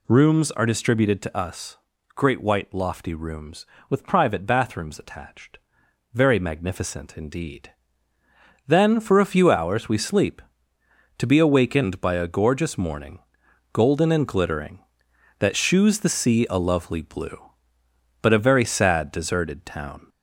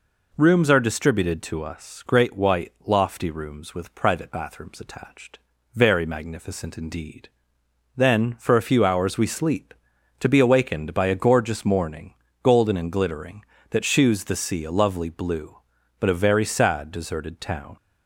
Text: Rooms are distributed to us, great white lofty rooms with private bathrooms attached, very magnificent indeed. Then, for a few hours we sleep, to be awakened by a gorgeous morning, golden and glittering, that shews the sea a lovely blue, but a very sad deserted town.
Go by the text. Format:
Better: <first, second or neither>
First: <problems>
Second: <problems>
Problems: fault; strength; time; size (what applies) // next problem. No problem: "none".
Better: second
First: gets louder; slight; throughout; 3 dB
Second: none